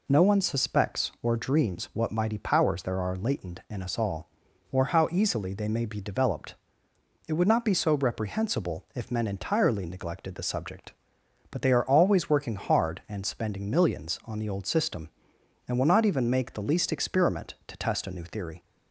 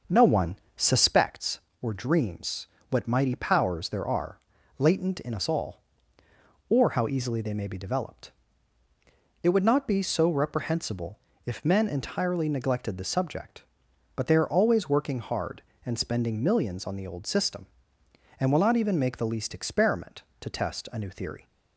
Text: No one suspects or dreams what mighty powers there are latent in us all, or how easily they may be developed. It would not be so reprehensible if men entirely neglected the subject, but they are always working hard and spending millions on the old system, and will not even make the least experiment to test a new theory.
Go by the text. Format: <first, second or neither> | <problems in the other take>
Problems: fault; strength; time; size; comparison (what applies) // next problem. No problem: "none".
first | starts louder than the rest; until 1.2 s; 6.5 dB // pauses between "one" and "suspects"; slight; at 0.5 s; 0.20 s long // pauses between "dreams" and "what"; slight; at 2.6 s; 0.24 s long // pauses between "are" and "latent"; at 4.3 s; 0.40 s long // pauses between "reprehensible" and "if"; slight; at 11.1 s; 0.26 s long